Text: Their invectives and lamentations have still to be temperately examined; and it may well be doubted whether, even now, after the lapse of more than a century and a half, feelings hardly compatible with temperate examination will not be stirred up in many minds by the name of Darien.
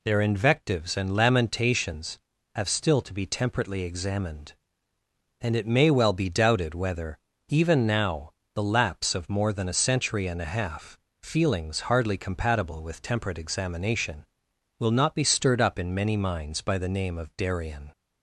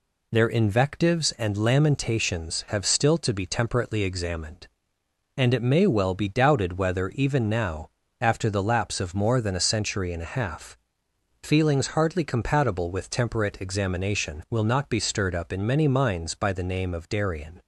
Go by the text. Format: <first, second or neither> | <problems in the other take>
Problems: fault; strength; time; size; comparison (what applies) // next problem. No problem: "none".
second | skips "after"; at 8.4 s